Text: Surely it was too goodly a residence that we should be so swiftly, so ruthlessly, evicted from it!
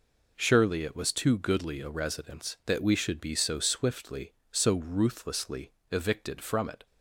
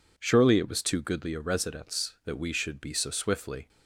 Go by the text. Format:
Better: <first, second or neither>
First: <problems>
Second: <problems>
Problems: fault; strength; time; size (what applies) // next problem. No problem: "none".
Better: first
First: none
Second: stops before "so ruthlessly evicted from it"; at 3.6 s